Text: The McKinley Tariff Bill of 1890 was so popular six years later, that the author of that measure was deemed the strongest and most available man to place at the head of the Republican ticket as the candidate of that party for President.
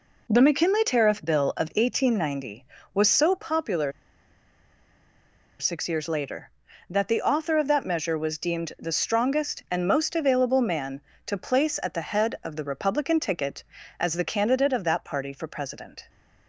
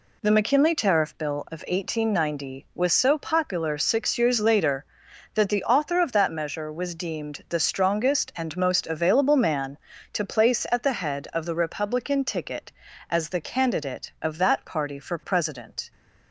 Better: second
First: pauses between "popular" and "six"; strong; at 3.9 s; 1.6 s long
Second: none

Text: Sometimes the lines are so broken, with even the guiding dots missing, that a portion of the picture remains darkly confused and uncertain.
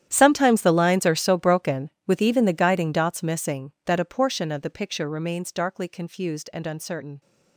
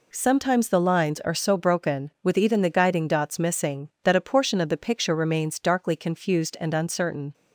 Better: second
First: gets quieter; strong; throughout; 18.5 dB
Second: none

